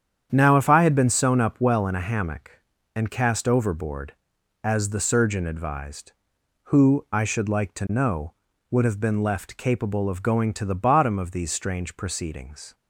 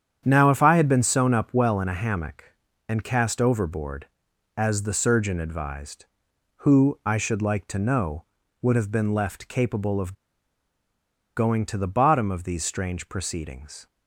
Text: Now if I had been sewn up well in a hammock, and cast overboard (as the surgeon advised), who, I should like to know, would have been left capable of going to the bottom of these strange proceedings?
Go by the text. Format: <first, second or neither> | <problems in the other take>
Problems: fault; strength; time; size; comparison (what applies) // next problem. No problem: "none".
first | starts louder than the rest; strong; until 1.2 s; 8.5 dB; strong in the first // pauses between "of" and "going"; at 10.1 s; 1.2 s long